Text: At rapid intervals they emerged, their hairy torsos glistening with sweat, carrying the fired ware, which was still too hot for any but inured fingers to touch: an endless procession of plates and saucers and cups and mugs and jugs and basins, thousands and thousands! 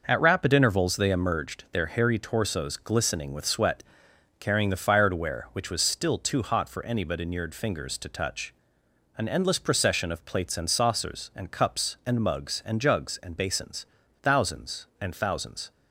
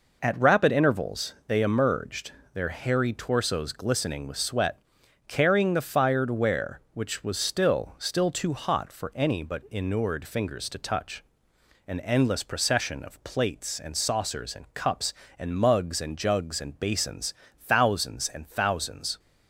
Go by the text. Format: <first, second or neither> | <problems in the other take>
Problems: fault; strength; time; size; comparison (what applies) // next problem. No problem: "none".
first | says "still" twice; at 7.9 s